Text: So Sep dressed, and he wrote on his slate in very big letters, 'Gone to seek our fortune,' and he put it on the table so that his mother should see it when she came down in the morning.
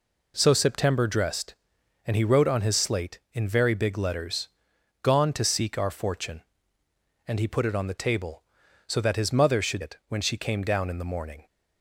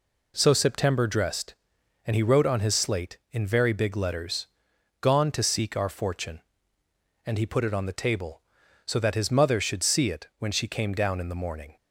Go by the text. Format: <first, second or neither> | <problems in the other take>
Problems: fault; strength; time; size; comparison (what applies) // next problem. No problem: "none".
second | skips "see"; at 9.8 s